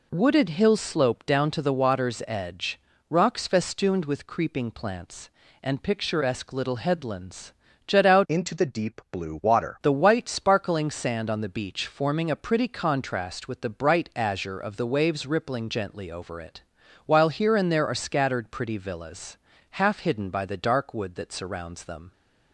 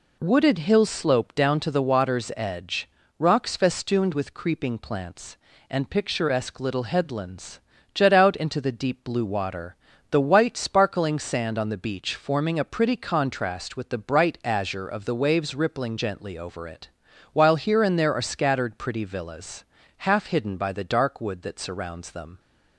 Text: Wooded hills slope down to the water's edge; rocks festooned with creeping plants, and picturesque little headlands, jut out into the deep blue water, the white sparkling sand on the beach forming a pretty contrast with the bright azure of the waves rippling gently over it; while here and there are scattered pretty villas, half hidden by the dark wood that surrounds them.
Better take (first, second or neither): second